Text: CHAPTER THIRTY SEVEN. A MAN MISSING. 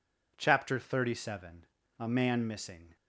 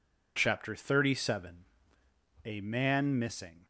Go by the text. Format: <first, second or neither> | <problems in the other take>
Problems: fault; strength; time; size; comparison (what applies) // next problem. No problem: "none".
neither | none